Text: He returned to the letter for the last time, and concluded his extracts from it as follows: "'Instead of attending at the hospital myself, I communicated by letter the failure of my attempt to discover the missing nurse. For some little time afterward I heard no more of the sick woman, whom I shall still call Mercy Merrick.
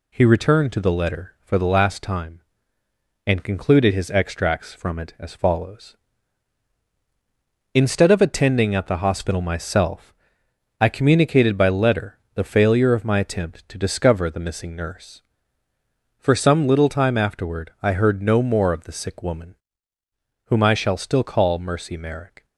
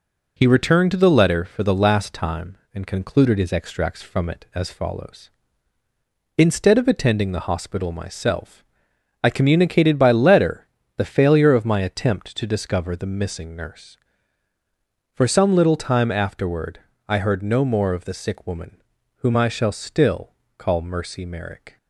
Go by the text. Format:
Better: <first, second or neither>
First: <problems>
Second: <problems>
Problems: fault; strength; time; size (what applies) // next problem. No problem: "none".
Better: first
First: pauses between "letter" and "the"; slight; at 12.1 s; 0.16 s long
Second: skips "at"; at 7.3 s // pauses between "letter" and "the"; slight; at 10.6 s; 0.30 s long // pauses between "afterward" and "I"; slight; at 16.8 s; 0.28 s long // pauses between "still" and "call"; slight; at 20.3 s; 0.26 s long